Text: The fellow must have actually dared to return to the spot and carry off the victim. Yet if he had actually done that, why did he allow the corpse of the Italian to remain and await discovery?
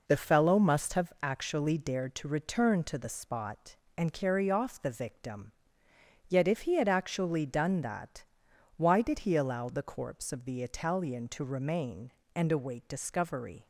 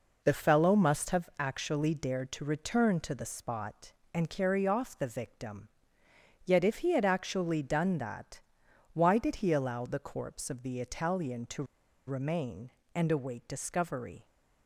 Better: first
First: none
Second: pauses between "to" and "remain"; at 11.6 s; 0.42 s long

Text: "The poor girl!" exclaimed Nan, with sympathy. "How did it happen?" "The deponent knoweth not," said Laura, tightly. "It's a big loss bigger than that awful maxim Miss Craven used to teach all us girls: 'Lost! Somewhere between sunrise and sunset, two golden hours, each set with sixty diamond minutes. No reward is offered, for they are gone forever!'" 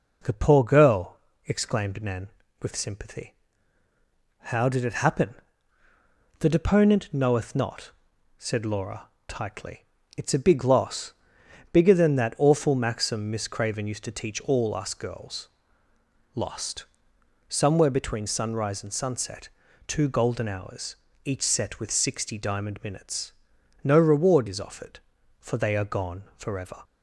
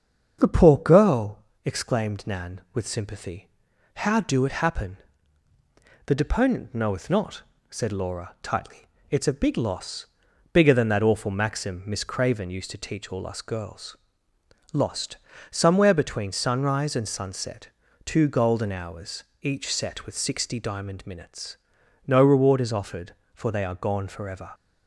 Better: first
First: pauses between "loss" and "bigger"; noticeable; at 11.1 s; 0.58 s long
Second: starts louder than the rest; until 1.4 s; 7 dB // says "do" for "did"; at 4.2 s // pauses between "loss" and "bigger"; noticeable; at 10.0 s; 0.48 s long

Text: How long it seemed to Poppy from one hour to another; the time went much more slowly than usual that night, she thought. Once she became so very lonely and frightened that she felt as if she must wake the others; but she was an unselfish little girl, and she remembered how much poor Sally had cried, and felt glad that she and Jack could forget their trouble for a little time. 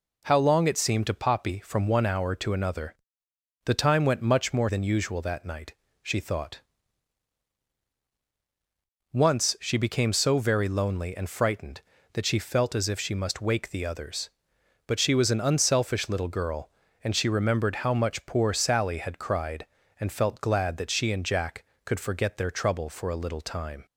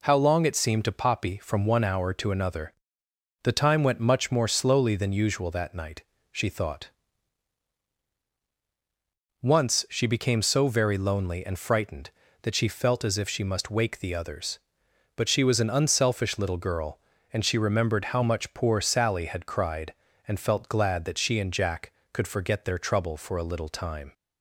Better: second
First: skips "slowly"; at 4.6 s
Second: none

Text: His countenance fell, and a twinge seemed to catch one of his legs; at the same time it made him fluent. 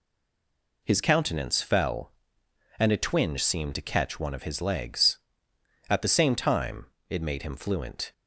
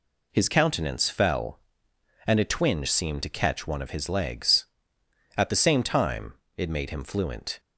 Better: second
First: stays silent before the first word; slight; until 0.8 s; 0.8 s long // pauses between "time" and "it"; slight; at 6.8 s; 0.22 s long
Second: pauses between "time" and "it"; slight; at 6.3 s; 0.22 s long

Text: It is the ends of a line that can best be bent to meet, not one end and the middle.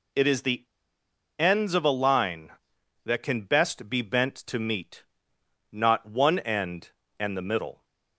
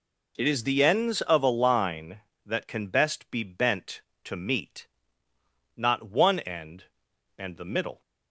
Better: second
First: pauses between "the" and "ends"; noticeable; at 0.6 s; 0.75 s long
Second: none

